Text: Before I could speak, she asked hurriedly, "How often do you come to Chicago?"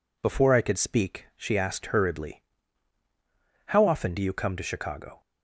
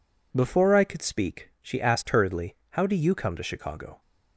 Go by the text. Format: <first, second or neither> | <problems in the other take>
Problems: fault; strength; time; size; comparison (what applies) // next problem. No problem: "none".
first | skips "often"; at 2.8 s